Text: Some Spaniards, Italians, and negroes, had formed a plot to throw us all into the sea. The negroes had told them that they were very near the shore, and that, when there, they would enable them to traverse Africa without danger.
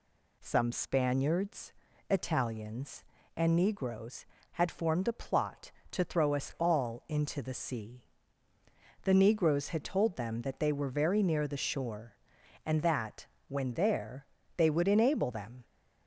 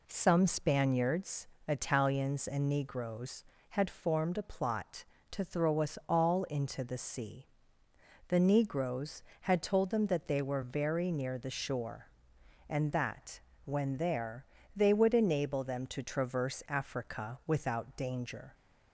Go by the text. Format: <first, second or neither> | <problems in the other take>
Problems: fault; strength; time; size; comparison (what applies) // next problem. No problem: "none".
second | stops before "to traverse Africa without danger"; at 15.6 s